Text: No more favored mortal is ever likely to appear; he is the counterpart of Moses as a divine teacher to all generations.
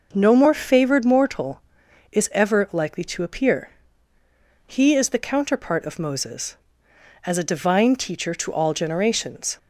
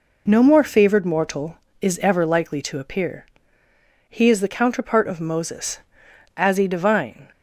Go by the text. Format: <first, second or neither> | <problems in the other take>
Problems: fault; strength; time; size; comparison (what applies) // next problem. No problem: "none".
first | stops before "teacher to all generations"; at 7.3 s